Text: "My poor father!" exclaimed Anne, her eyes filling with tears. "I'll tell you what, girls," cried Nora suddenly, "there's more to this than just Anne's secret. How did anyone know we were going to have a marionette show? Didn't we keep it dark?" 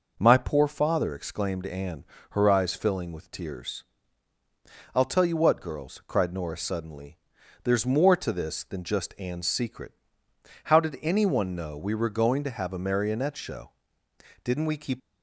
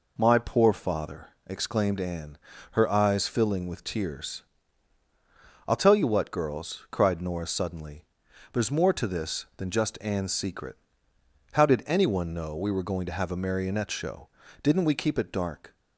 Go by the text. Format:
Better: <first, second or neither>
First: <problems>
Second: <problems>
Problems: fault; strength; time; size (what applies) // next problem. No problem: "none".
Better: second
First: stops before "it dark"; at 15.0 s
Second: none